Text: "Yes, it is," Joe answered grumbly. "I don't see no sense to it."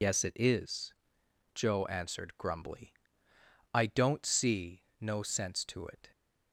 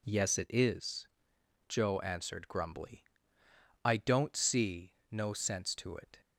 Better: second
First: loses the start of "Yes"; at 0.0 s; 120 ms // pauses between "see" and "no"; slight; at 4.8 s; 0.18 s long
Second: pauses between "see" and "no"; slight; at 4.9 s; 0.18 s long

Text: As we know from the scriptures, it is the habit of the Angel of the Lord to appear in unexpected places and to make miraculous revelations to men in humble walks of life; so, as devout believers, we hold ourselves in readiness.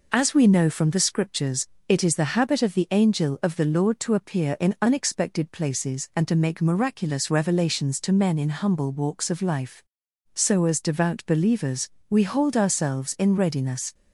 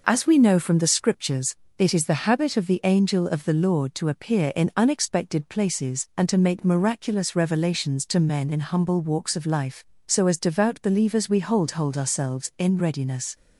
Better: first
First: none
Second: says "hold" twice; at 11.7 s

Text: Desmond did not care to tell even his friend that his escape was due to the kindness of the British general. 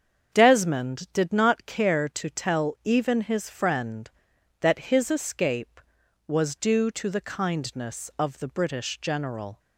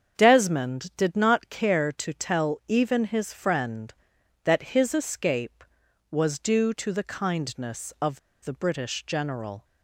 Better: first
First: starts louder than the rest; strong; until 1.3 s; 7 dB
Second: starts louder than the rest; strong; until 1.1 s; 7 dB // pauses between "of" and "the"; slight; at 8.1 s; 0.24 s long

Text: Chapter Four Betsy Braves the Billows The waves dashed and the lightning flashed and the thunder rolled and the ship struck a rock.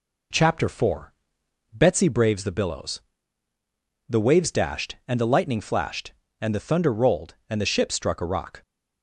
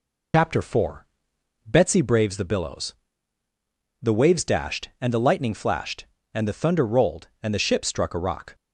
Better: first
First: pauses between "Four" and "Betsy"; noticeable; at 1.1 s; 0.62 s long // pauses between "Billows" and "The"; at 3.0 s; 1.0 s long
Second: loses the start of "Chapter"; at 0.3 s; 105 ms // pauses between "Four" and "Betsy"; noticeable; at 1.0 s; 0.62 s long // pauses between "Billows" and "The"; at 2.9 s; 1.0 s long

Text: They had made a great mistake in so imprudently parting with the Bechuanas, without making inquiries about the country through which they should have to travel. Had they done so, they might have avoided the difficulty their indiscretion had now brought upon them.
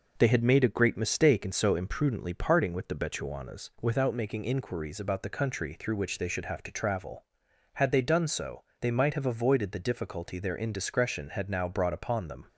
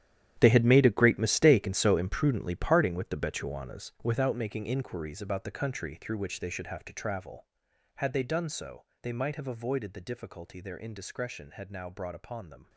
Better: first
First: none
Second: gets quieter; strong; throughout; 15 dB

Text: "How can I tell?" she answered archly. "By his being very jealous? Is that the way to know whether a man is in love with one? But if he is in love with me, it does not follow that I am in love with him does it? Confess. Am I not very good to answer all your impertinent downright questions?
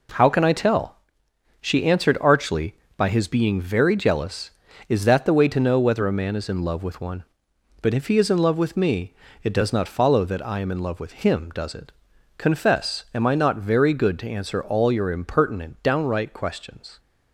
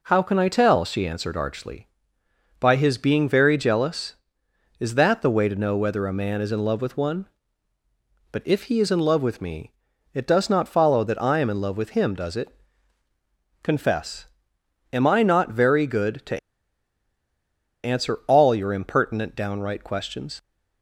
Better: first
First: none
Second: pauses between "to" and "answer"; strong; at 16.3 s; 1.4 s long

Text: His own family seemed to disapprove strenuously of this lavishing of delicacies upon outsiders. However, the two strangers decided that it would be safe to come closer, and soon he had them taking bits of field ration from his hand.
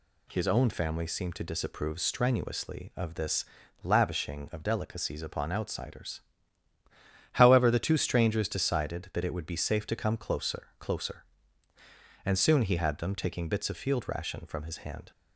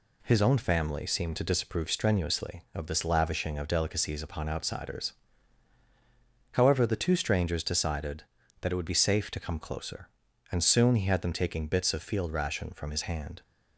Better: second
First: pauses between "this" and "lavishing"; at 3.4 s; 0.38 s long // says "closer" twice; at 10.7 s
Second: none

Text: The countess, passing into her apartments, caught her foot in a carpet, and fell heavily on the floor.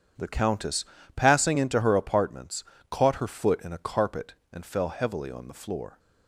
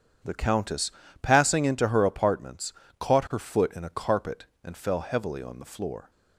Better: neither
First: starts louder than the rest; strong; until 1.4 s; 8.5 dB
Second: starts louder than the rest; strong; until 1.5 s; 8.5 dB

